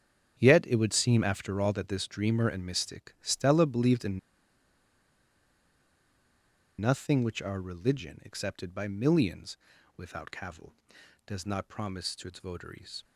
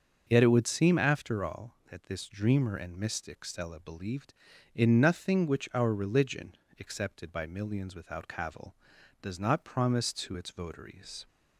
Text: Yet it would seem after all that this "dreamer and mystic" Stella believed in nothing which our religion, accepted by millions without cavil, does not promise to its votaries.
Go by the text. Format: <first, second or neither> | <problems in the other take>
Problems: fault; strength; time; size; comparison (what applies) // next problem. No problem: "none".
second | starts louder than the rest; strong; until 1.3 s; 8 dB; also in the second // pauses between "in" and "nothing"; strong; at 4.1 s; 2.6 s long // pauses between "millions" and "without"; at 9.5 s; 0.40 s long